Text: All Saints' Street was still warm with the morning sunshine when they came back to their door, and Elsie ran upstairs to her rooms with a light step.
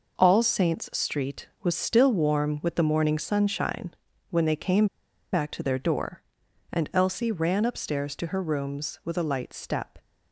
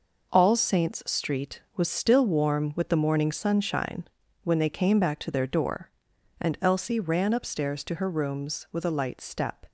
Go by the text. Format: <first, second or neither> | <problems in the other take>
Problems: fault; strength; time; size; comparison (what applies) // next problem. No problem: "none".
second | pauses between "sunshine" and "when"; slight; at 3.9 s; 0.36 s long; slight in the second // pauses between "came" and "back"; noticeable; at 4.8 s; 0.47 s long